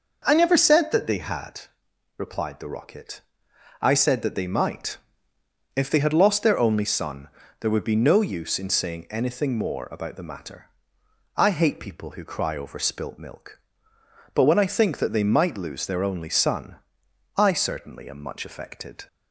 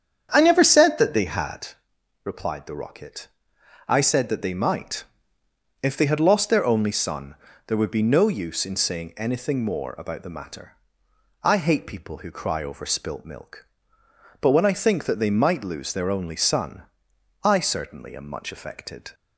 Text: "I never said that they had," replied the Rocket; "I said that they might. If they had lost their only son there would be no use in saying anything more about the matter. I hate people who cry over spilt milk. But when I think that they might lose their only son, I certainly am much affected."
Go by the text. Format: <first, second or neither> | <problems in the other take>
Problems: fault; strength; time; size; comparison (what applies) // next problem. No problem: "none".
first | starts louder than the rest; strong; until 1.8 s; 8.5 dB // pauses between "son" and "there"; slight; at 7.3 s; 0.32 s long; slight in the first